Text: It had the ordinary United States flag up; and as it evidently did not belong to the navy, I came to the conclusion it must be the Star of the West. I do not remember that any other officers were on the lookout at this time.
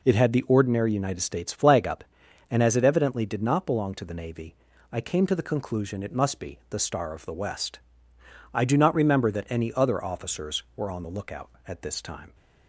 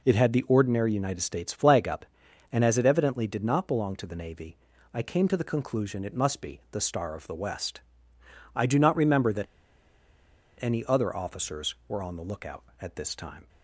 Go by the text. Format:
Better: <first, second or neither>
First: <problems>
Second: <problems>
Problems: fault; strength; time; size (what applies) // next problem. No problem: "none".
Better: first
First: none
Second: pauses between "that" and "any"; at 9.4 s; 1.1 s long